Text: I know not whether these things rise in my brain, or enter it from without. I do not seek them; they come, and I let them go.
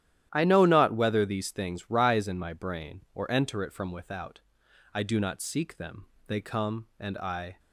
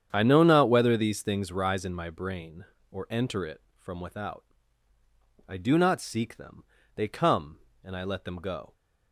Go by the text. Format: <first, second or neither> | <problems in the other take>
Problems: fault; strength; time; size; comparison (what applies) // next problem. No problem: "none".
second | starts louder than the rest; strong; until 1.3 s; 12 dB; strong in the second // stops before "let them go"; at 7.5 s